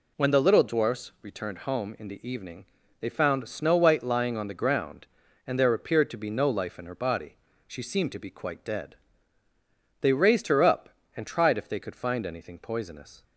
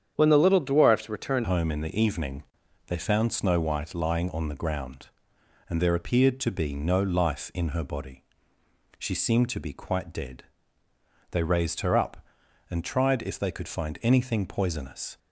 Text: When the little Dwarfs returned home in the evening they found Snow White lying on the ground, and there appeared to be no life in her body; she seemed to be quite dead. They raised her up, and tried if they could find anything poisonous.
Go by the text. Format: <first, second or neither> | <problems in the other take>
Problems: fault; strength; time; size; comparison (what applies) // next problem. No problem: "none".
first | starts louder than the rest; strong; until 1.1 s; 8.5 dB // changes voice at "home"; from 1.4 s on; 13.7 s long // pauses between "evening" and "they"; at 2.4 s; 0.42 s long; slight in the first